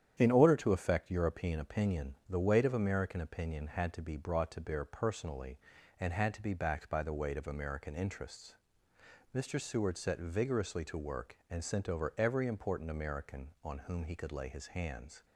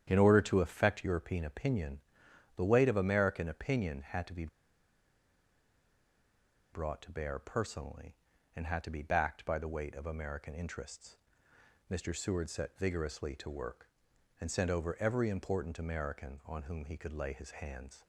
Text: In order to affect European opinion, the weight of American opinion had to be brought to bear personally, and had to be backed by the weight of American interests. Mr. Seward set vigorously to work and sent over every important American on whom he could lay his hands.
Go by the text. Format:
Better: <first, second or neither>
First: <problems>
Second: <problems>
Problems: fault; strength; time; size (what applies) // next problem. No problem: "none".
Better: first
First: starts louder than the rest; strong; until 1.2 s; 9.5 dB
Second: starts louder than the rest; strong; until 1.0 s; 9.5 dB // pauses between "be" and "brought"; strong; at 4.4 s; 2.2 s long